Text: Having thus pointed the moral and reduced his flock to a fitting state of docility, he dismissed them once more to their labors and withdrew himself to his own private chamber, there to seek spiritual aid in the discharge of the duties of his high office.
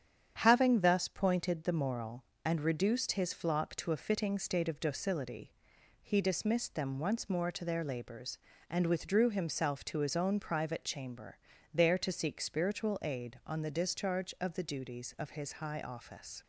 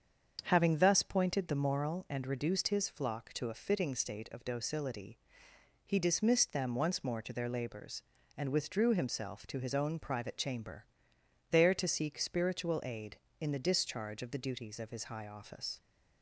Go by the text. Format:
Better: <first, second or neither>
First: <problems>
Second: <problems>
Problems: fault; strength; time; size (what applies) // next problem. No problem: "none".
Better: second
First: starts louder than the rest; strong; until 1.4 s; 8.5 dB // says "on" for "in"; at 13.4 s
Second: starts louder than the rest; strong; until 1.4 s; 7 dB